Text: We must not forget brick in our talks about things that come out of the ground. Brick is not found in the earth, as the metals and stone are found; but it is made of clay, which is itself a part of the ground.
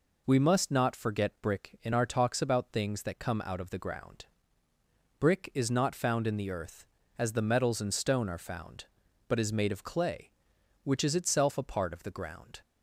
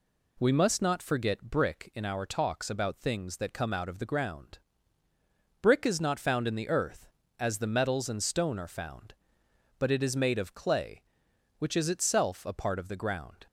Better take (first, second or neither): second